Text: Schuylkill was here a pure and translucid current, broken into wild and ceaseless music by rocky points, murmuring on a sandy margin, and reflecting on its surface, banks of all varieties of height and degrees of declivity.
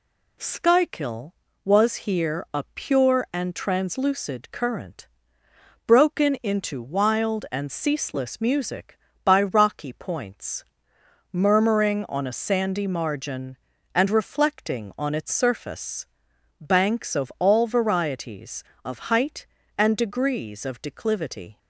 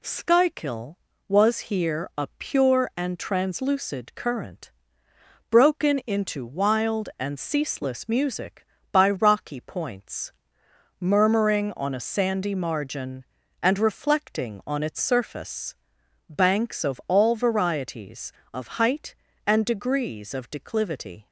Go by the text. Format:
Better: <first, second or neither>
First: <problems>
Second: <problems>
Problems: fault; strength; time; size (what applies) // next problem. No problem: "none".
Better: neither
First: none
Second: none